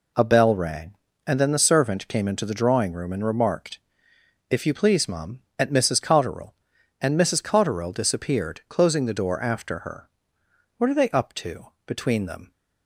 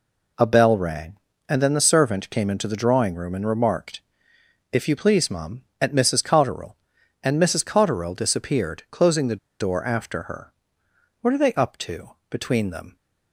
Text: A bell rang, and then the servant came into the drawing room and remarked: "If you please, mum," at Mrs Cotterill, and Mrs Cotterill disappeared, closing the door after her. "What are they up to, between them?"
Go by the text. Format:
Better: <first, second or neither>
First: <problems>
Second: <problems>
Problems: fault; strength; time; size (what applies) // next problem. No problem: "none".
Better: first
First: none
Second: pauses between "the" and "door"; slight; at 9.3 s; 0.21 s long